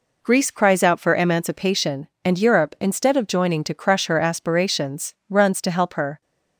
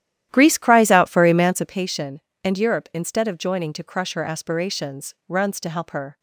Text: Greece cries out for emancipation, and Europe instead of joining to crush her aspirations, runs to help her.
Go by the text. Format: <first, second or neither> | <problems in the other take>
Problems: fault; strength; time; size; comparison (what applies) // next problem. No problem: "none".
first | starts louder than the rest; strong; until 1.9 s; 12 dB